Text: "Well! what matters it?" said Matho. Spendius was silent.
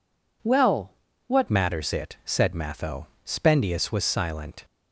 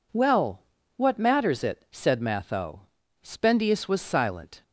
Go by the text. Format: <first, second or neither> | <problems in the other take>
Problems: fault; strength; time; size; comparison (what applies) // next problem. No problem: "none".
second | changes voice at "matters"; from 1.4 s on; 3.2 s long